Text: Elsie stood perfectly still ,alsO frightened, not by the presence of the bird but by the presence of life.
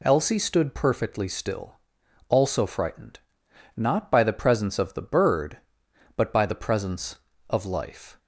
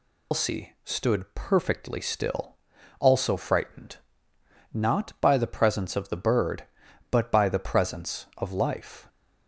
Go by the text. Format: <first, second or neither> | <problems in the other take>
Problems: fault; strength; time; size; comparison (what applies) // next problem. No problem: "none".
first | loses the start of "Elsie"; at 0.3 s; 145 ms